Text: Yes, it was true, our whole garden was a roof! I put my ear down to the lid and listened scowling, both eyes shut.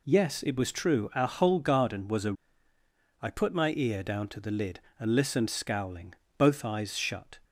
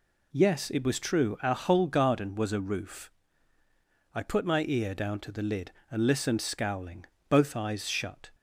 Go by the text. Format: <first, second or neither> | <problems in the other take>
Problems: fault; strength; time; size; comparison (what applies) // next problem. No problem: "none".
second | skips "roof"; at 2.7 s